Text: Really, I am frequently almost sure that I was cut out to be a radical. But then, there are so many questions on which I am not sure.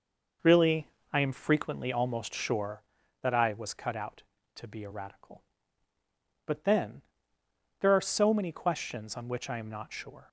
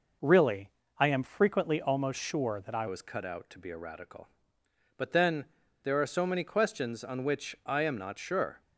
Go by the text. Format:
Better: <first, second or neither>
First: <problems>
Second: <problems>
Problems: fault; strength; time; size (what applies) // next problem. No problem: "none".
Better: first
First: none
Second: changes voice at "was"; from 2.8 s on; 5.8 s long